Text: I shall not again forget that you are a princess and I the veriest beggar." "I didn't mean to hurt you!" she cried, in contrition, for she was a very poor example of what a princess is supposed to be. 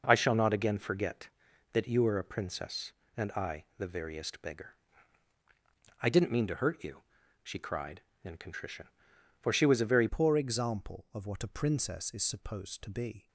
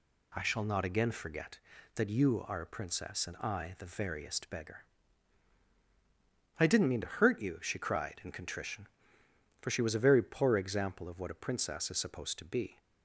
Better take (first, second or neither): second